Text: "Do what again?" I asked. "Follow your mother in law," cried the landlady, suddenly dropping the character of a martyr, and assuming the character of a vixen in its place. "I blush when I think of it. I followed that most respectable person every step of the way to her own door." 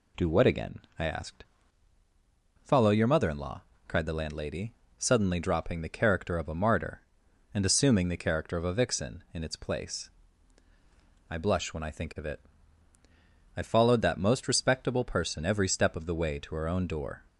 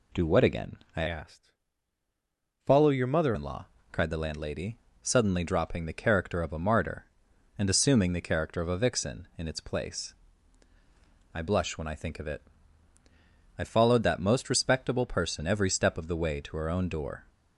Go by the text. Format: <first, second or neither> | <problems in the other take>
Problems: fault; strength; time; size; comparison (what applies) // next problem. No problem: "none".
first | changes voice from "asked" to "mother"; from 1.0 to 3.3 s; 2.3 s long